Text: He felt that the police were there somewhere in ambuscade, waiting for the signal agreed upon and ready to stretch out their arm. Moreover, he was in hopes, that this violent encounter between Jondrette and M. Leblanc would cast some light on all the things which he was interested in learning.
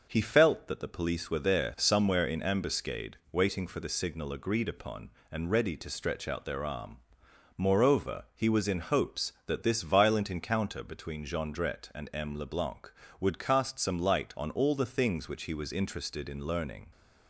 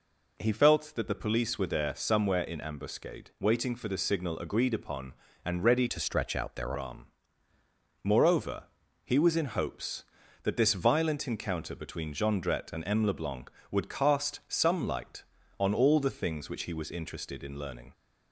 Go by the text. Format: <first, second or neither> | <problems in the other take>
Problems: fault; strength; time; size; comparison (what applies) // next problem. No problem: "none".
first | changes voice from "to" to "their"; from 5.8 to 6.7 s; 0.9 s long